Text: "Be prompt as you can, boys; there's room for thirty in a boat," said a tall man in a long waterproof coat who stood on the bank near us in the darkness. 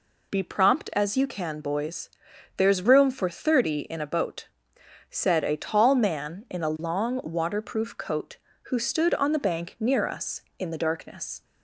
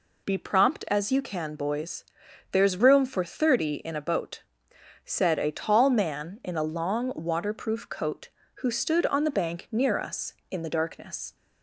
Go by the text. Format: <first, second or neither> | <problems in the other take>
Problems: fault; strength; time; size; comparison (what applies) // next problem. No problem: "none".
neither | none